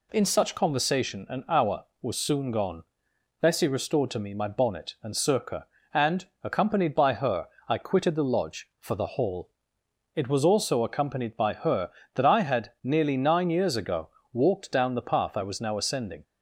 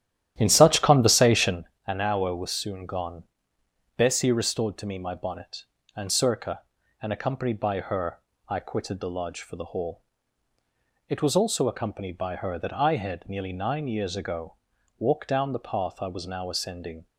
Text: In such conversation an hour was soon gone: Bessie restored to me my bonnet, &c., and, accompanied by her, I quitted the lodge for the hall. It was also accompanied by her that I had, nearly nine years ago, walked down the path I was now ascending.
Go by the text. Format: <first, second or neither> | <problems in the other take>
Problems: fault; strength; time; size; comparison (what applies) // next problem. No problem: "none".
first | starts louder than the rest; strong; until 1.6 s; 11.5 dB // pauses between "conversation" and "an"; slight; at 1.6 s; 0.22 s long